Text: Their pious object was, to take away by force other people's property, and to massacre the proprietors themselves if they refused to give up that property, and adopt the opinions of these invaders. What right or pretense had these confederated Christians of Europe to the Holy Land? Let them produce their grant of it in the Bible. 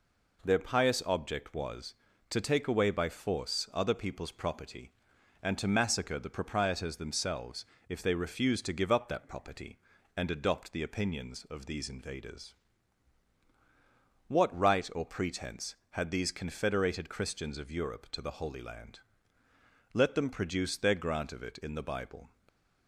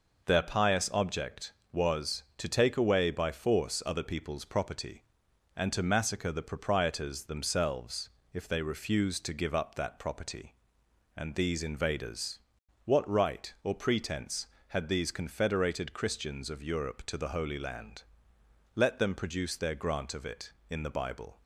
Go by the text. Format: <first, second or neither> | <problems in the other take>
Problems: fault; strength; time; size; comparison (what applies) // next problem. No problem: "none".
first | pauses between "themselves" and "if"; slight; at 8.0 s; 0.24 s long; slight in the first // skips "adopt the opinions of"; at 11.3 s